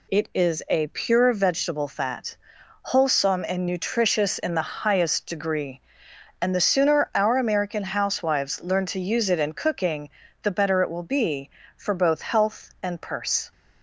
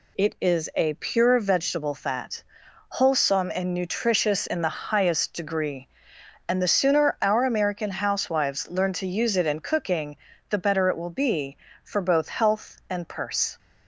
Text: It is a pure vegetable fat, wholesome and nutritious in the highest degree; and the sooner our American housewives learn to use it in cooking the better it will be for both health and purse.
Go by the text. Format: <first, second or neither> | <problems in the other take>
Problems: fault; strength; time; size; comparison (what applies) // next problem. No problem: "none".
neither | pauses between "cooking" and "the"; slight; the same in both